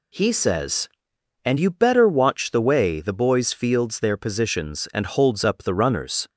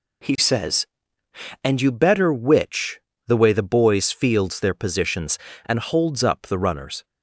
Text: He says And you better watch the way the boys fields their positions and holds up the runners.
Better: first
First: none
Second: says "witch" for "watch"; at 2.3 s

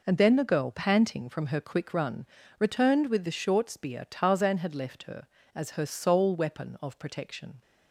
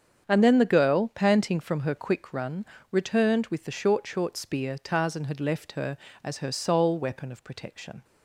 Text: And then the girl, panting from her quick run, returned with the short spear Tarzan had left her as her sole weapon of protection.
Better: first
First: none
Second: starts louder than the rest; strong; until 1.2 s; 7 dB // says "short" twice; at 4.0 s

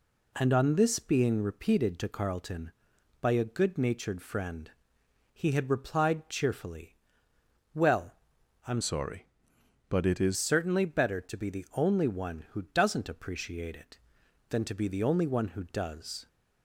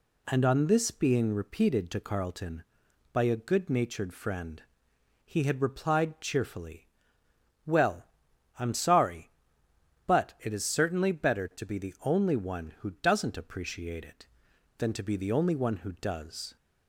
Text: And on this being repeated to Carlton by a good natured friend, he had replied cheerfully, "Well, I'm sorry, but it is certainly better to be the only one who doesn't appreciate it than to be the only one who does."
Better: second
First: changes voice from "sorry" to "is"; from 8.8 to 10.3 s; 1.5 s long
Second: none

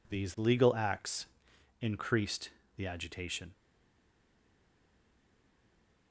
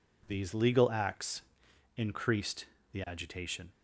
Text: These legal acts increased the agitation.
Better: second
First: pauses between "acts" and "increased"; noticeable; at 1.2 s; 0.54 s long // pauses between "increased" and "the"; slight; at 2.4 s; 0.28 s long // stays silent after the last word; strong; from 3.5 s on; 2.6 s long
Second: pauses between "acts" and "increased"; noticeable; at 1.4 s; 0.54 s long // pauses between "increased" and "the"; slight; at 2.6 s; 0.28 s long

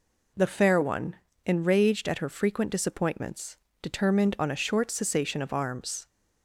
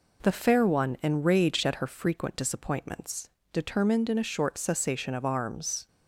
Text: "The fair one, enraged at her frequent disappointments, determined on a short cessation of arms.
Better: first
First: none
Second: says "in" for "on"; at 4.0 s

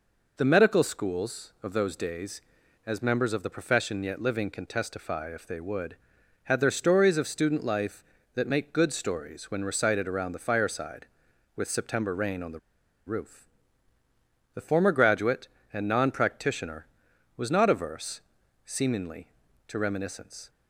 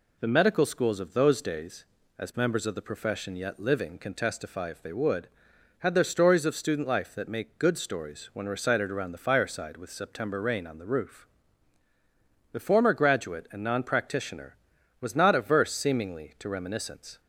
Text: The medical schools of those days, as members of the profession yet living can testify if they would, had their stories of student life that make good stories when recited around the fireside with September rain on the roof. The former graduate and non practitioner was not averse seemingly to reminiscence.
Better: second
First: pauses between "the" and "roof"; noticeable; at 12.5 s; 0.48 s long // pauses between "averse" and "seemingly"; at 18.2 s; 0.44 s long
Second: none

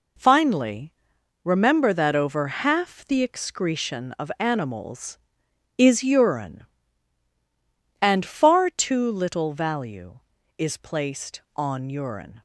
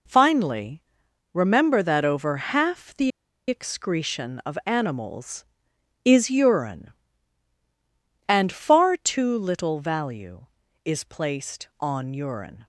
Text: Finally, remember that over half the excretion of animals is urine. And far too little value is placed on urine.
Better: first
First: none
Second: pauses between "the" and "excretion"; at 3.1 s; 0.37 s long

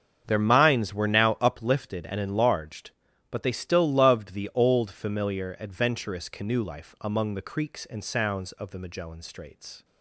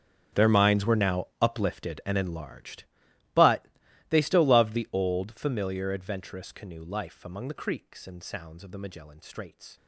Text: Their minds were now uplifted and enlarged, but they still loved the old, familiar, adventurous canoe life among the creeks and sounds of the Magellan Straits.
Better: first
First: starts louder than the rest; until 1.2 s; 7 dB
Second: gets quieter; strong; throughout; 18 dB // starts louder than the rest; strong; until 1.4 s; 7.5 dB // pauses between "but" and "they"; at 3.6 s; 0.42 s long

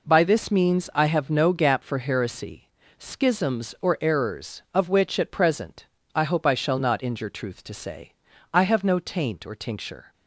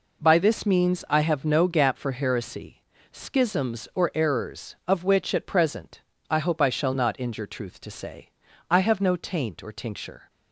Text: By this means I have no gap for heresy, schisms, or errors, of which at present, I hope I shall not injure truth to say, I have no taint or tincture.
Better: neither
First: none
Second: none

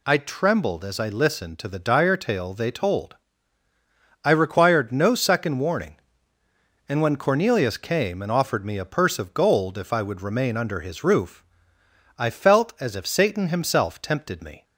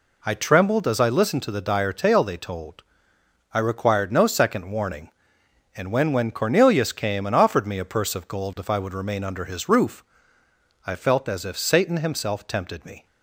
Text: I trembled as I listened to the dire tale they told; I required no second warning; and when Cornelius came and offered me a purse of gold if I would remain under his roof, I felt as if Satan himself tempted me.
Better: first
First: none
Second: says "when" twice; at 6.1 s

